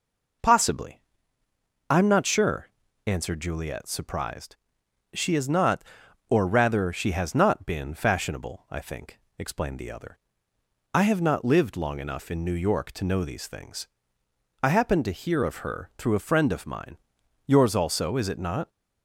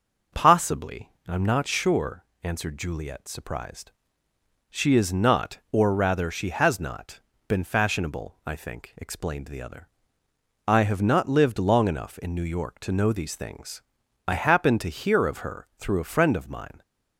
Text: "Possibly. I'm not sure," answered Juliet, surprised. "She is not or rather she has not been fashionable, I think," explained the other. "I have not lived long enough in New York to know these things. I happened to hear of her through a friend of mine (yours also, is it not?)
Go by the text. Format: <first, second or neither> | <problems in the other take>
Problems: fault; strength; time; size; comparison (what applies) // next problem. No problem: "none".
first | starts louder than the rest; until 1.5 s; 6 dB // pauses between "not" and "been"; slight; at 7.1 s; 0.28 s long // stops before "yours also is it not"; at 16.8 s